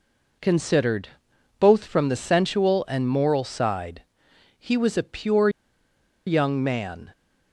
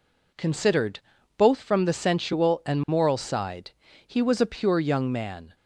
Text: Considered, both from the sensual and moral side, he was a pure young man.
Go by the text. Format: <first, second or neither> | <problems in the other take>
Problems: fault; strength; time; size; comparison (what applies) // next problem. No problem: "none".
second | pauses between "pure" and "young"; noticeable; at 5.4 s; 0.78 s long